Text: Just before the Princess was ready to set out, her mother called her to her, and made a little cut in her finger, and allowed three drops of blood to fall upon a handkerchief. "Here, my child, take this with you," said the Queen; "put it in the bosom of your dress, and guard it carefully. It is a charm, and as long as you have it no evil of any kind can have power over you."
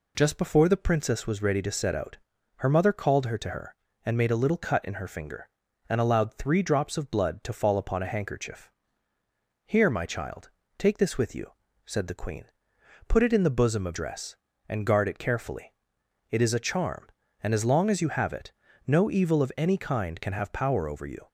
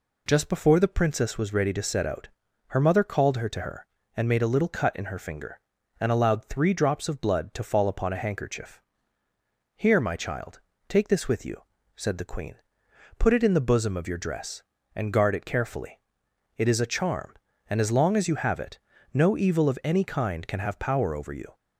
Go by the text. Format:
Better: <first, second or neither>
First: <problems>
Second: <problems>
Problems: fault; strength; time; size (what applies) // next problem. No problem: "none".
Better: second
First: skips "your"; at 13.9 s // pauses between "it" and "no"; slight; at 18.5 s; 0.34 s long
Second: pauses between "it" and "no"; slight; at 18.8 s; 0.34 s long